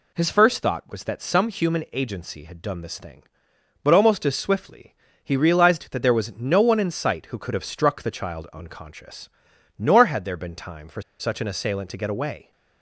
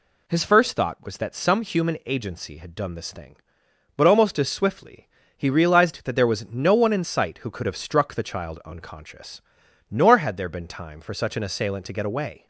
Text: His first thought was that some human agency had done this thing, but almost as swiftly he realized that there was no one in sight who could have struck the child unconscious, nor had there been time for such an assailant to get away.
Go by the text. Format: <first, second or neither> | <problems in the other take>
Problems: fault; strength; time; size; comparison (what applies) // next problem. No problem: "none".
second | pauses between "swiftly" and "he"; slight; at 4.9 s; 0.28 s long; slight in the second // pauses between "for" and "such"; slight; at 11.0 s; 0.19 s long